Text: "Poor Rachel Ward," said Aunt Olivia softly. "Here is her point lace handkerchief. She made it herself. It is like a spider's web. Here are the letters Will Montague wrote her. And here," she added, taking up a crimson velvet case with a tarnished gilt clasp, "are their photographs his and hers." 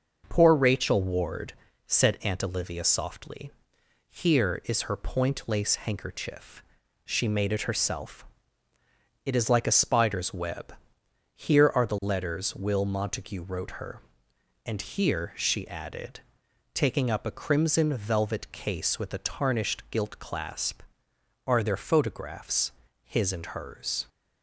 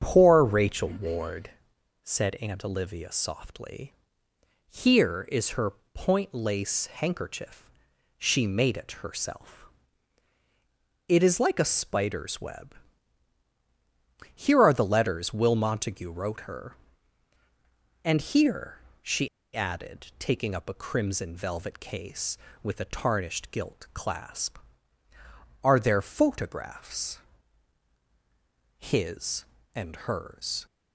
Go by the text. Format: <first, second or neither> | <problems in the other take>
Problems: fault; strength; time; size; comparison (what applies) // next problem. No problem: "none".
first | starts louder than the rest; strong; until 1.0 s; 7.5 dB // pauses between "her" and "point"; slight; at 5.7 s; 0.24 s long // pauses between "she" and "added"; slight; at 19.2 s; 0.27 s long // pauses between "photographs" and "his"; strong; at 27.1 s; 1.6 s long; slight in the first